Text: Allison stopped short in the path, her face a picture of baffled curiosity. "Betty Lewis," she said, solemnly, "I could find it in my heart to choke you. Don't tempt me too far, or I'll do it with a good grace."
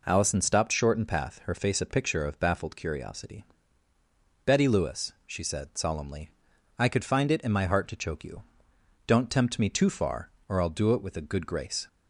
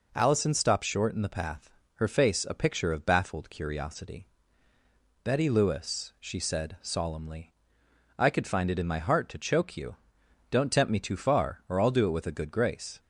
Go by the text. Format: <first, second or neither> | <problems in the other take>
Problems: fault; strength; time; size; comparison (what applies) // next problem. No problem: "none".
second | skips "the"; at 1.0 s